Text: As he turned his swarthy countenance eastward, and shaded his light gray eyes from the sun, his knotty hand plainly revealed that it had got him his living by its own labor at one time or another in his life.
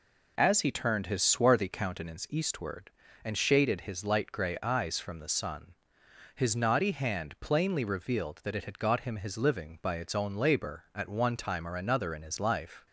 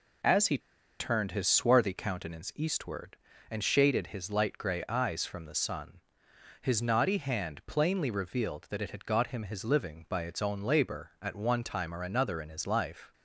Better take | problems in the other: first | pauses between "he" and "turned"; at 0.5 s; 0.41 s long

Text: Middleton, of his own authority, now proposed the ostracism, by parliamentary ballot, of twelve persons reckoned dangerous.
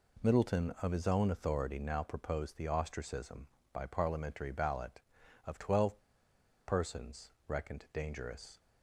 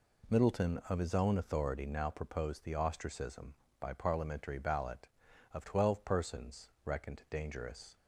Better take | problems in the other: second | pauses between "twelve" and "persons"; noticeable; at 5.9 s; 0.67 s long // pauses between "persons" and "reckoned"; slight; at 7.3 s; 0.16 s long

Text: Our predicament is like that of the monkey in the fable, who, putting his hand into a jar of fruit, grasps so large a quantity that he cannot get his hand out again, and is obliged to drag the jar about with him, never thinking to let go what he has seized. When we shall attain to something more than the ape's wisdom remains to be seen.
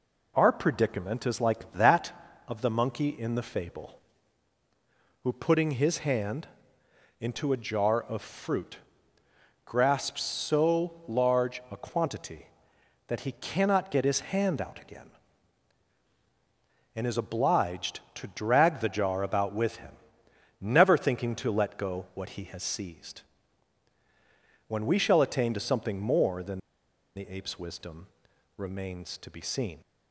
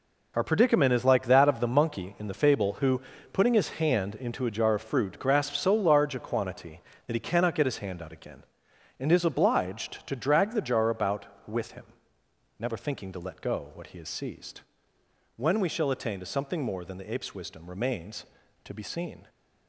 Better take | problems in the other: second | pauses between "hand" and "into"; noticeable; at 6.4 s; 0.74 s long // pauses between "than" and "the"; noticeable; at 26.5 s; 0.56 s long // pauses between "wisdom" and "remains"; noticeable; at 28.0 s; 0.48 s long

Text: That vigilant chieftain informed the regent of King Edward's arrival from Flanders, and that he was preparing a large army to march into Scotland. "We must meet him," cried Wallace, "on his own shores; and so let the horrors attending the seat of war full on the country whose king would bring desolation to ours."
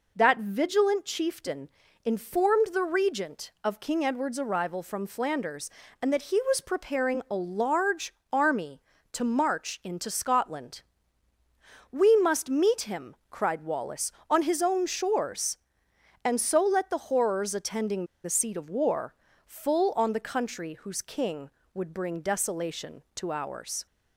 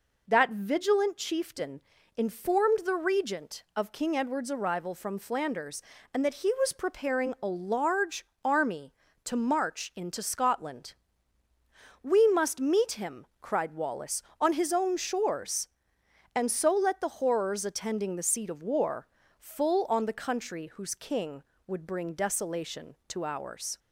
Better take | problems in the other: second | pauses between "chieftain" and "informed"; slight; at 1.6 s; 0.34 s long; slight in the second // pauses between "large" and "army"; slight; at 8.1 s; 0.20 s long; slight in the second // pauses between "attending" and "the"; slight; at 18.0 s; 0.20 s long // pauses between "war" and "full"; slight; at 19.1 s; 0.32 s long; slight in the second

